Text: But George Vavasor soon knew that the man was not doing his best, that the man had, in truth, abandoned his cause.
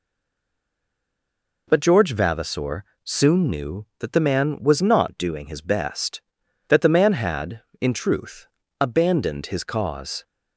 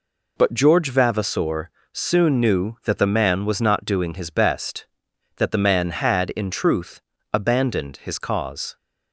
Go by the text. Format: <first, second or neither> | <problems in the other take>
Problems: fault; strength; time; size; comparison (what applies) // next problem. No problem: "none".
second | stays silent before the first word; noticeable; until 1.6 s; 1.6 s long // pauses between "Vavasor" and "soon"; slight; at 2.8 s; 0.22 s long; slight in the second